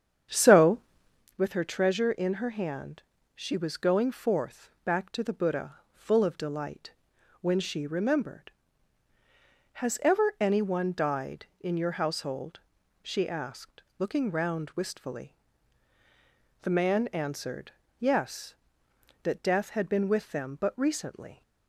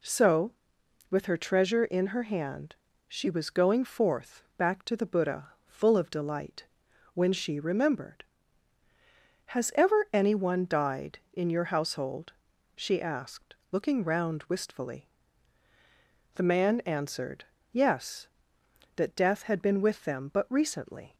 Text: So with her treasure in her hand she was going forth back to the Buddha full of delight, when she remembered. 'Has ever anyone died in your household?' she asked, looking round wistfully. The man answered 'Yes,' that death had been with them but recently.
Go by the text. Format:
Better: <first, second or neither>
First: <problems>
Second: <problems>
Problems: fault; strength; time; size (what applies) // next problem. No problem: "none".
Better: second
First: starts louder than the rest; strong; until 1.3 s; 8 dB // pauses between "hand" and "she"; slight; at 3.0 s; 0.32 s long // pauses between "Buddha" and "full"; slight; at 5.7 s; 0.16 s long // pauses between "answered" and "Yes"; slight; at 17.7 s; 0.26 s long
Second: pauses between "hand" and "she"; slight; at 2.7 s; 0.32 s long // pauses between "Buddha" and "full"; slight; at 5.5 s; 0.16 s long // pauses between "answered" and "Yes"; slight; at 17.4 s; 0.26 s long